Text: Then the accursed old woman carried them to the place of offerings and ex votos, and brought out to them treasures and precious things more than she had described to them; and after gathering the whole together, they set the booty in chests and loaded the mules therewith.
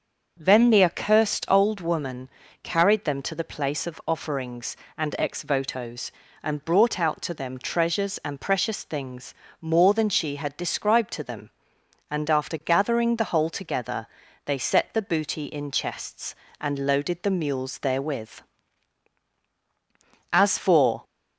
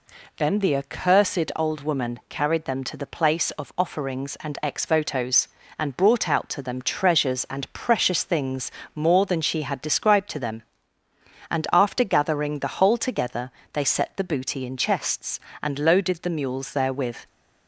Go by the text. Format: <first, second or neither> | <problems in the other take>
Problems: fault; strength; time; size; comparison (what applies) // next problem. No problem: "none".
second | starts louder than the rest; until 1.4 s; 6.5 dB // pauses between "woman" and "carried"; slight; at 2.2 s; 0.34 s long // pauses between "things" and "more"; slight; at 9.3 s; 0.26 s long; slight in the second // goes on to say "As for"; noticeable; from 20.3 s on; 0.72 s long